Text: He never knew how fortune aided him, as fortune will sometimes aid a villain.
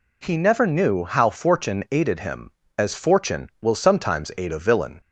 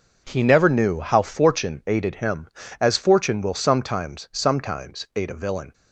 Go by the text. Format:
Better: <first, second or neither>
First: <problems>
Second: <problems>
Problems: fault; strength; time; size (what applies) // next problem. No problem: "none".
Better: first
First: none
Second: says "sometimes" twice; at 4.3 s